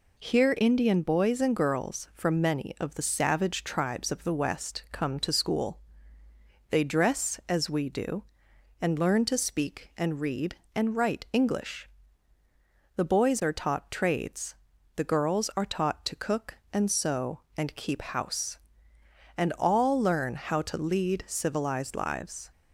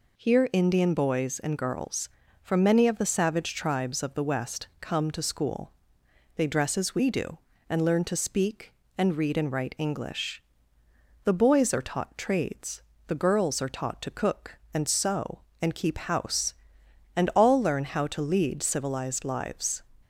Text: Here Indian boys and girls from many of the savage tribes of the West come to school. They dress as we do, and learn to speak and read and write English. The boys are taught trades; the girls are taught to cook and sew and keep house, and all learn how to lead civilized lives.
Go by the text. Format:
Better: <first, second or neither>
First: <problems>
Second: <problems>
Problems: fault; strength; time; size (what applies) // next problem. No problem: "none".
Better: neither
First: none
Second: none